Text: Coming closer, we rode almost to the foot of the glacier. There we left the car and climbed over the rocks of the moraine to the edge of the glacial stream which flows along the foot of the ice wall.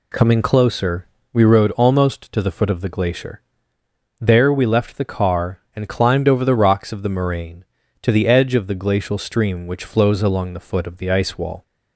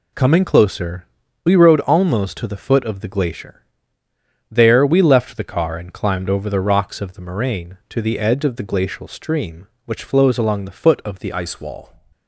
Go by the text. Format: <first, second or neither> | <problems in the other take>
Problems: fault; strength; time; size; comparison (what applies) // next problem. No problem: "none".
first | changes voice at "ice"; from 11.3 s on; 0.6 s long